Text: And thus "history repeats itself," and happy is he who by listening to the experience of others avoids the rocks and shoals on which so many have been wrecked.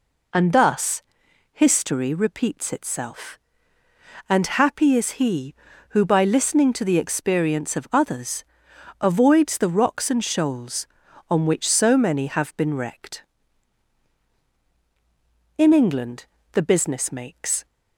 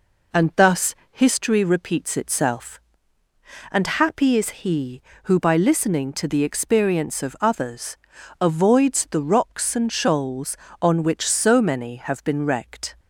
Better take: second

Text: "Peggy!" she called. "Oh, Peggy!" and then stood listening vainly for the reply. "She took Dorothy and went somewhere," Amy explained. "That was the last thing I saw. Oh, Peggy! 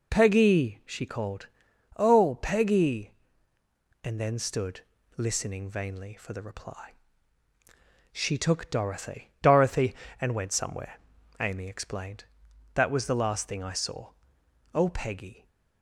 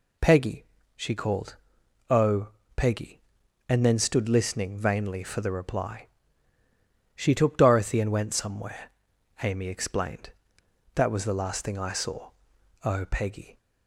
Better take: second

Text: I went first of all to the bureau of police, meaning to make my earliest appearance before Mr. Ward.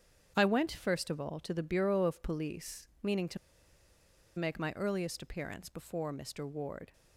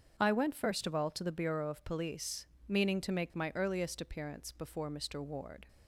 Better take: second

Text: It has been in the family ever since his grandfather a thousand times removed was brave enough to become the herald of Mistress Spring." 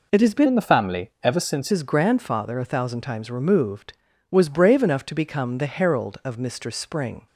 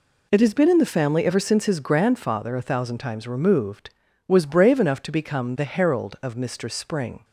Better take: second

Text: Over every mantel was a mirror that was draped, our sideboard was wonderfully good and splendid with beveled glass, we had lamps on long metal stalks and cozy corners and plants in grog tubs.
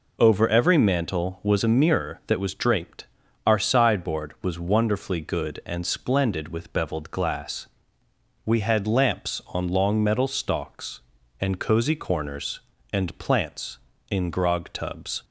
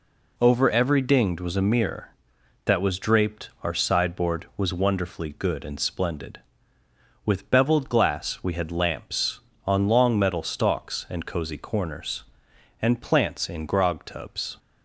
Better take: first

